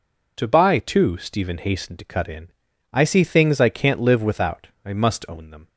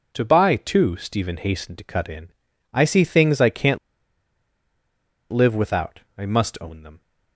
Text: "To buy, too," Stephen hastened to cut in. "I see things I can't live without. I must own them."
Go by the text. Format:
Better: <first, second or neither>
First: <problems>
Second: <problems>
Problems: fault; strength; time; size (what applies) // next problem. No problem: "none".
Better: first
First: none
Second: pauses between "can't" and "live"; strong; at 3.7 s; 1.5 s long